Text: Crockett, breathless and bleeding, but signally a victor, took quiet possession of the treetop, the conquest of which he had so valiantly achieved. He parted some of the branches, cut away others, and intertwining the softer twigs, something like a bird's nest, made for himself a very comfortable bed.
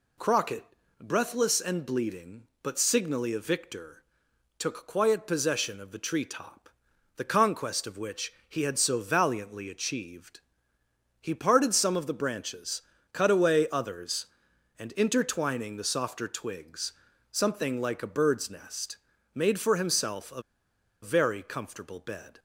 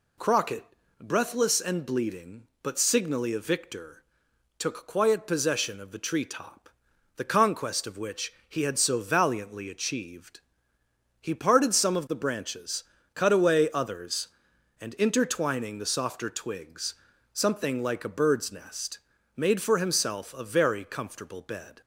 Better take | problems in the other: second | pauses between "which" and "he"; slight; at 8.3 s; 0.16 s long; slight in the second // pauses between "a" and "very"; noticeable; at 20.4 s; 0.60 s long

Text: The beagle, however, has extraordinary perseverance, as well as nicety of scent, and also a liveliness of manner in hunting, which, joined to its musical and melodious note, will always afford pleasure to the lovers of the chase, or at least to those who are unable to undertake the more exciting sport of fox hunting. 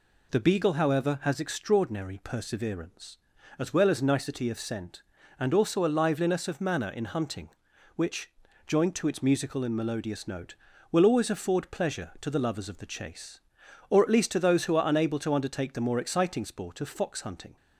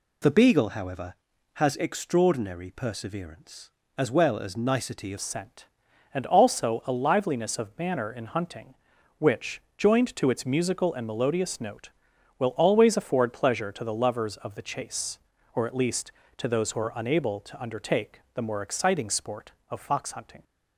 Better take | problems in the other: first | changes voice at "scent"; from 5.1 s on; 15.3 s long

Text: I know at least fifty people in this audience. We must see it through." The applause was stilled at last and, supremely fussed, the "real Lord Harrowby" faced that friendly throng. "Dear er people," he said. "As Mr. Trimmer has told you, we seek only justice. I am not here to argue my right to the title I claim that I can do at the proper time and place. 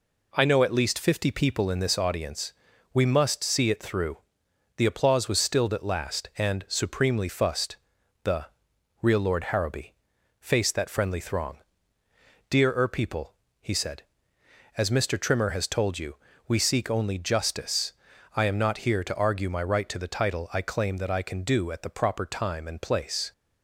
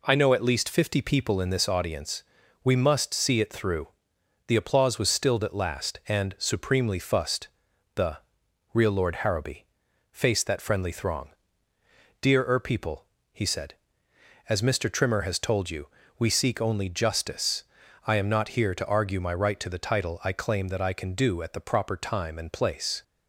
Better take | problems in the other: neither | pauses between "the" and "real"; noticeable; the same in both // pauses between "Harrowby" and "faced"; noticeable; the same in both

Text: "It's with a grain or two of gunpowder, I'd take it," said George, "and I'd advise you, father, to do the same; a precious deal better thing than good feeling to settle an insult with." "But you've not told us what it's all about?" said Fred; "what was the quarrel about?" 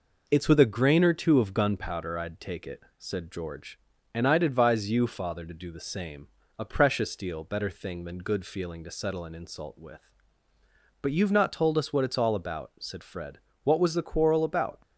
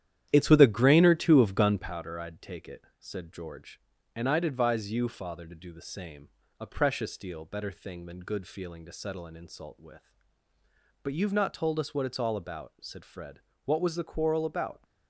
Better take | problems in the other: first | starts louder than the rest; strong; until 2.0 s; 10.5 dB

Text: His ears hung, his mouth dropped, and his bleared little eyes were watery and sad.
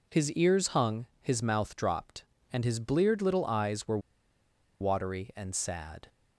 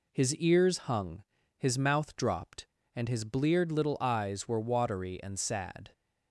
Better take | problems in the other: second | pauses between "were" and "watery"; noticeable; at 3.9 s; 0.82 s long

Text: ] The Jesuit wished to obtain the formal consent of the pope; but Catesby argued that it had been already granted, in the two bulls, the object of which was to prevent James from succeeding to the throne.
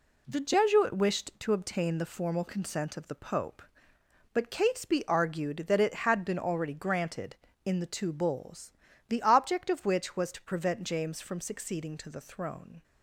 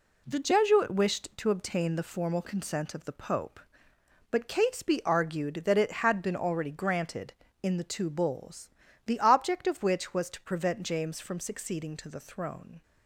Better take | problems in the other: neither | none

